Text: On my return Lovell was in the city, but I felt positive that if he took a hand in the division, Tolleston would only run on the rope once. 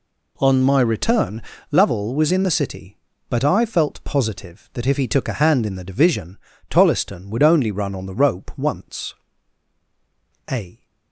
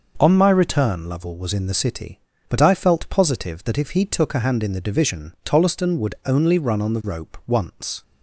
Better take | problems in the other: second | pauses between "return" and "Lovell"; slight; at 1.4 s; 0.30 s long // goes on to say "A"; slight; from 10.5 s on; 0.34 s long

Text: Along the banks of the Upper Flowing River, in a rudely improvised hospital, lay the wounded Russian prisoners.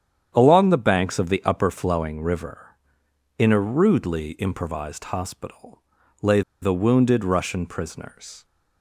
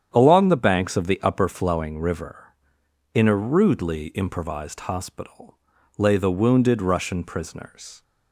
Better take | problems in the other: second | starts louder than the rest; strong; until 1.3 s; 9 dB; strong in the second // pauses between "lay" and "the"; slight; at 6.4 s; 0.21 s long

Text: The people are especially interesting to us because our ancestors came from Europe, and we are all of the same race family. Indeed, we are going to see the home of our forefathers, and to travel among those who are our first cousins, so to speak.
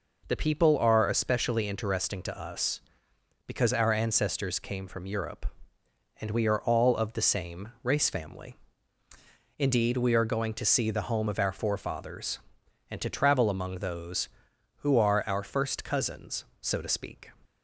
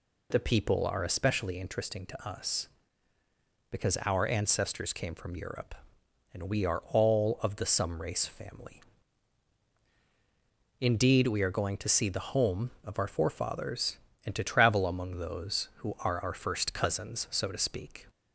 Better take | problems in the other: first | says "some" for "same"; at 7.6 s

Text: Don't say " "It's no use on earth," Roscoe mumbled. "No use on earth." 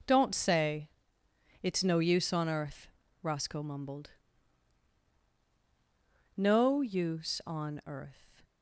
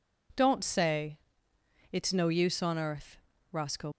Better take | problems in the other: first | stops before "mumbled No use on earth"; at 3.9 s

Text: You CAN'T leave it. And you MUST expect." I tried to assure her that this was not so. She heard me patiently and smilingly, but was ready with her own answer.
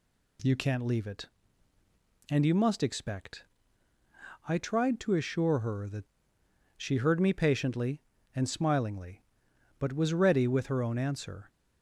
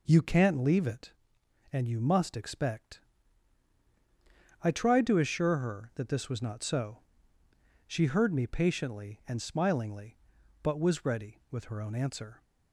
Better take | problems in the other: second | skips "this was not so"; at 6.4 s

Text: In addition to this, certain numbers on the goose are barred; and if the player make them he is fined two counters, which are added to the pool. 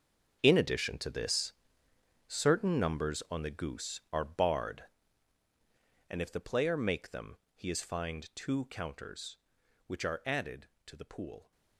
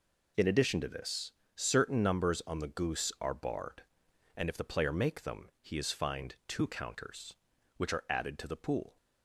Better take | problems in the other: second | gets quieter; strong; throughout; 15 dB // pauses between "them" and "he"; slight; at 7.3 s; 0.22 s long

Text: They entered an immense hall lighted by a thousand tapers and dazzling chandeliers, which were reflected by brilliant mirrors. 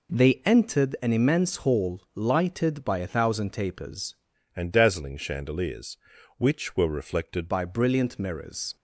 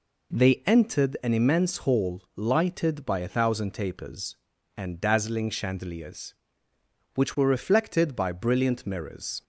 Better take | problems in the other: second | pauses between "hall" and "lighted"; slight; at 2.0 s; 0.16 s long; slight in the second // changes voice from "and" to "reflected"; from 4.5 to 7.4 s; 2.9 s long

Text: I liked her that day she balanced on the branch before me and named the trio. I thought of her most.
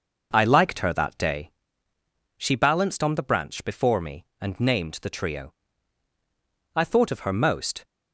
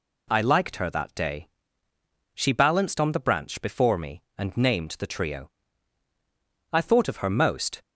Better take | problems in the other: second | starts louder than the rest; noticeable; until 1.4 s; 5.5 dB // pauses between "day" and "she"; noticeable; at 1.4 s; 0.88 s long; noticeable in the second

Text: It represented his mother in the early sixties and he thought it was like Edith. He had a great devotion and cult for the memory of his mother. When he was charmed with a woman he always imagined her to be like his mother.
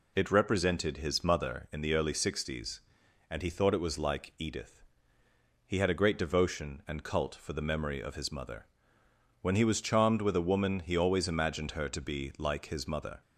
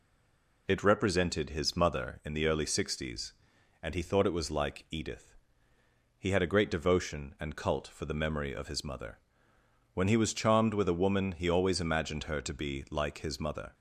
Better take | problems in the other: first | stays silent before the first word; slight; until 0.6 s; 0.6 s long

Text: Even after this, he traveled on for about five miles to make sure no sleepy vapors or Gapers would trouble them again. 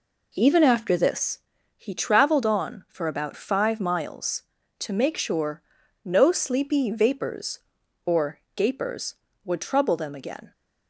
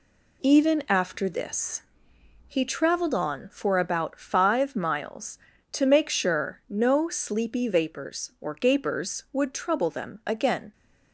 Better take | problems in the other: second | starts louder than the rest; until 1.3 s; 3.5 dB // pauses between "sure" and "no"; at 5.6 s; 0.42 s long // pauses between "or" and "Gapers"; slight; at 8.3 s; 0.16 s long

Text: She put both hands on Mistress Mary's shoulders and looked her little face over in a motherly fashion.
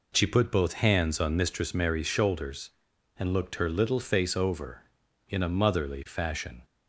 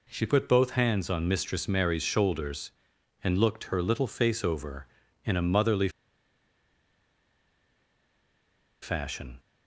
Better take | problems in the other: first | pauses between "motherly" and "fashion"; strong; at 5.8 s; 2.9 s long

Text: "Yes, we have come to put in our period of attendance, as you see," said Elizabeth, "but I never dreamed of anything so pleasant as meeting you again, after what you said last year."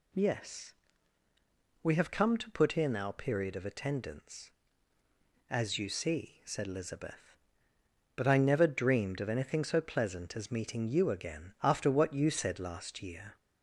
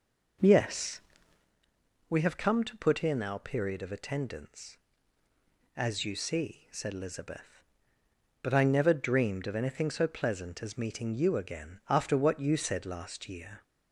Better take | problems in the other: first | starts louder than the rest; noticeable; until 1.5 s; 5 dB

